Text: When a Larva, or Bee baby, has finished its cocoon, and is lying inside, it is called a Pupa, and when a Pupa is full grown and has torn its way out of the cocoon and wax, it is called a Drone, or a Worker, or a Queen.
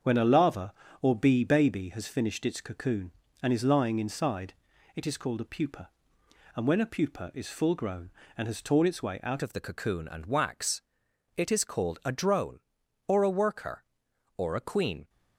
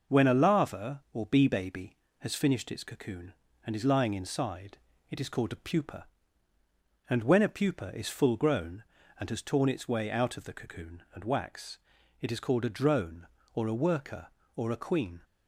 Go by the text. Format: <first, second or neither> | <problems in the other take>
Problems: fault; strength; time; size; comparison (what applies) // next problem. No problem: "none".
second | starts louder than the rest; until 1.2 s; 7 dB // changes voice at "of"; from 9.4 s on; 5.6 s long